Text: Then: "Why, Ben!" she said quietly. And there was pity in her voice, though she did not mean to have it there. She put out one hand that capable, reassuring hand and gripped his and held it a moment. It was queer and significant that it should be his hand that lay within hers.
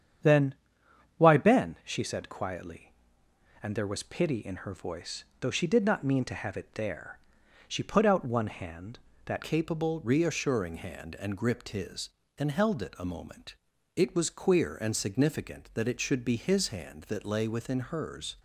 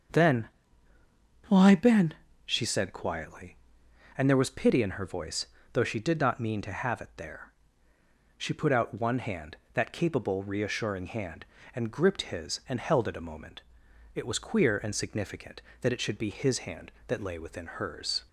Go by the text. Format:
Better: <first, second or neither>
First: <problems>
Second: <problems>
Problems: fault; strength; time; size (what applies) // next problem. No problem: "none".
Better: second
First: starts louder than the rest; strong; until 1.9 s; 8 dB // changes voice at "capable"; from 9.4 s on; 8.9 s long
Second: starts louder than the rest; until 2.1 s; 6.5 dB